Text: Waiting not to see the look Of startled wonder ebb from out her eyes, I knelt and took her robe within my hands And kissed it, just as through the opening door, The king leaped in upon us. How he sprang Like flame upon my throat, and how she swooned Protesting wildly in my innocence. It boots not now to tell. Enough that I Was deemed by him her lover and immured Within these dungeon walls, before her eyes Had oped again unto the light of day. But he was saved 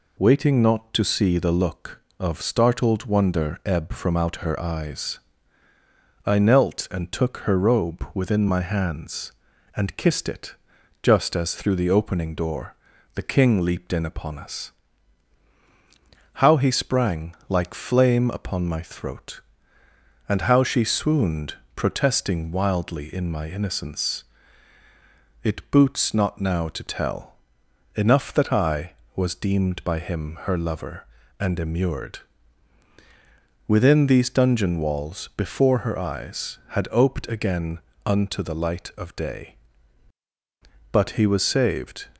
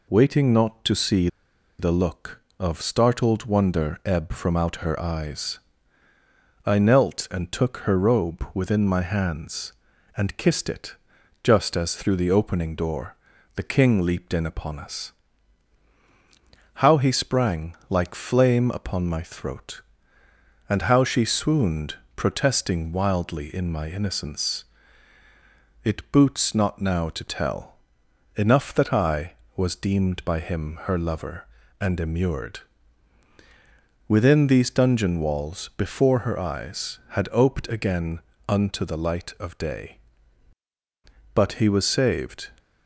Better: first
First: pauses between "swooned" and "Protesting"; slight; at 21.5 s; 0.18 s long // pauses between "immured" and "Within"; strong; at 32.2 s; 1.4 s long // pauses between "again" and "unto"; slight; at 37.8 s; 0.26 s long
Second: pauses between "see" and "the"; noticeable; at 1.2 s; 0.50 s long // pauses between "swooned" and "Protesting"; slight; at 21.9 s; 0.18 s long // pauses between "immured" and "Within"; strong; at 32.6 s; 1.4 s long // pauses between "again" and "unto"; slight; at 38.2 s; 0.28 s long

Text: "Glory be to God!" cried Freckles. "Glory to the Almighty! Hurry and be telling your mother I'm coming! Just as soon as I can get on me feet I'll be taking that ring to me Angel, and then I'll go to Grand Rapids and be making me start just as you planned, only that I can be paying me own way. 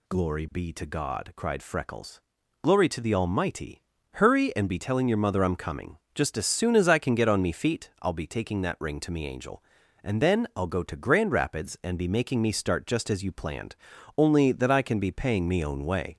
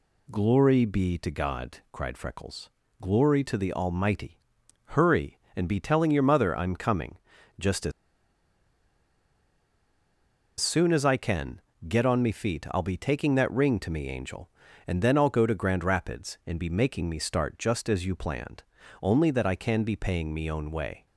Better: first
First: none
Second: pauses between "as" and "soon"; strong; at 7.9 s; 2.6 s long // pauses between "can" and "get"; slight; at 11.6 s; 0.26 s long

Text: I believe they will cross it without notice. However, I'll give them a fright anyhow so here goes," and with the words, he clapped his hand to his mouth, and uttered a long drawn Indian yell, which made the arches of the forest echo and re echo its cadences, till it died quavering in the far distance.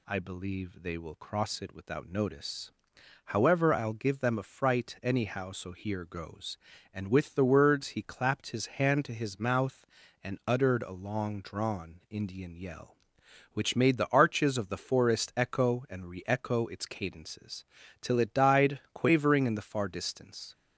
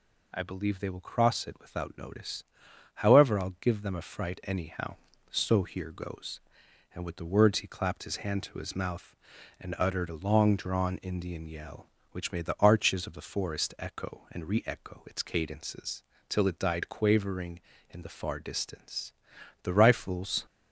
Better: first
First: none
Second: goes on to say "The rifles"; noticeable; from 19.6 s on; 0.82 s long

